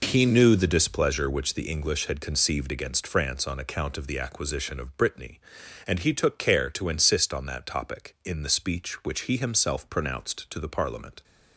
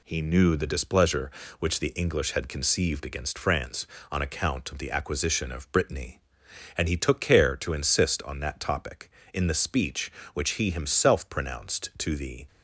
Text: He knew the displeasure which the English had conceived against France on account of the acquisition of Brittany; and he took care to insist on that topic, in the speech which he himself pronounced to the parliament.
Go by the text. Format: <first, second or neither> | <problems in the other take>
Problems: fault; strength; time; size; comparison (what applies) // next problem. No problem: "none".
first | stops before "parliament"; at 12.4 s